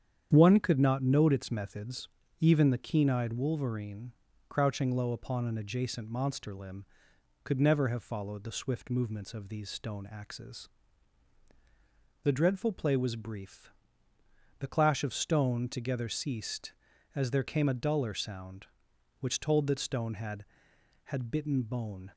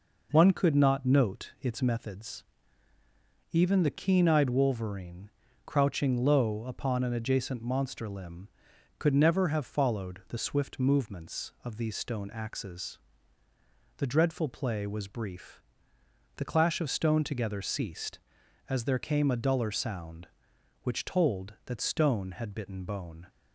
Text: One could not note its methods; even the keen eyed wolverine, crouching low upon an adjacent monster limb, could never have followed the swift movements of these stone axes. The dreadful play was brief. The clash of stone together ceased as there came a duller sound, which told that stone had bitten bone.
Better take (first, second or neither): second